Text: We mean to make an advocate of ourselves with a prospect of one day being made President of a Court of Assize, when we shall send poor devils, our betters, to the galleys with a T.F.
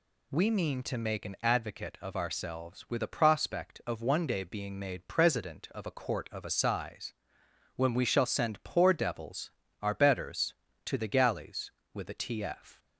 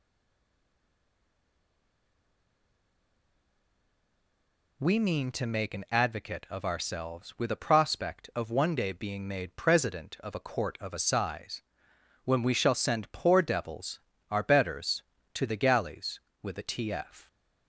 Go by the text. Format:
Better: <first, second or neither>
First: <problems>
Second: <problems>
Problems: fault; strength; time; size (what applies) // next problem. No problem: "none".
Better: first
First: none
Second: stays silent before the first word; strong; until 4.7 s; 4.7 s long